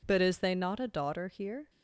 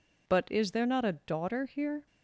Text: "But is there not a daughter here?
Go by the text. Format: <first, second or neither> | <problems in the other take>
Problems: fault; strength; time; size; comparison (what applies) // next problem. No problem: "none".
second | says "they" for "there"; at 0.3 s